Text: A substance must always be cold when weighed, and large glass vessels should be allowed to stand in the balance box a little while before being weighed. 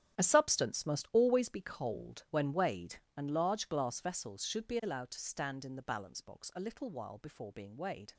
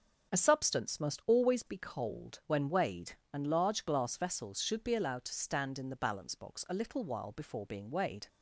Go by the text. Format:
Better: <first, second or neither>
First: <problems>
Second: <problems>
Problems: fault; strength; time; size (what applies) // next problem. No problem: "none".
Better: second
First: gets quieter; strong; throughout; 14 dB // starts louder than the rest; strong; until 1.2 s; 10.5 dB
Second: starts louder than the rest; strong; until 1.3 s; 7 dB